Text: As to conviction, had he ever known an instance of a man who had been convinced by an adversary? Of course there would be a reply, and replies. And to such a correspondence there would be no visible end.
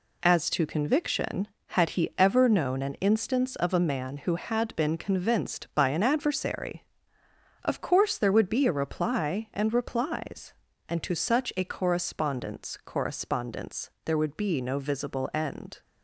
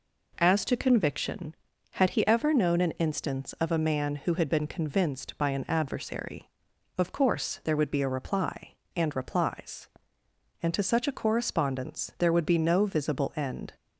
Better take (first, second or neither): second